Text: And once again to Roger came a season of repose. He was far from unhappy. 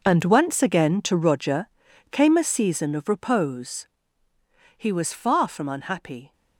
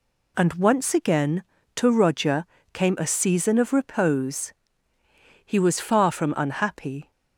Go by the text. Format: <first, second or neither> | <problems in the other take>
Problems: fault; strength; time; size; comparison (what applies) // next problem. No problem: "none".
second | gets quieter; strong; throughout; 14 dB // pauses between "Roger" and "came"; at 1.6 s; 0.42 s long; slight in the second